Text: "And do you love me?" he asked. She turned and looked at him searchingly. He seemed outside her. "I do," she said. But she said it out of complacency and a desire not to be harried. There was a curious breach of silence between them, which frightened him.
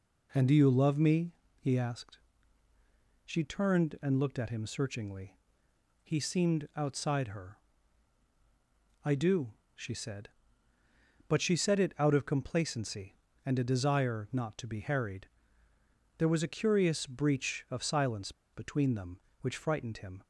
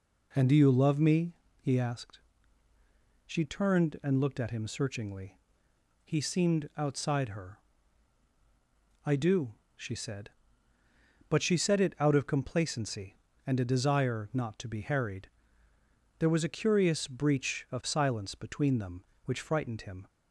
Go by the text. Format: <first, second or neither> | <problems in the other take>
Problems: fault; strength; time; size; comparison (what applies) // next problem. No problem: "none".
second | pauses between "silence" and "between"; slight; at 18.3 s; 0.22 s long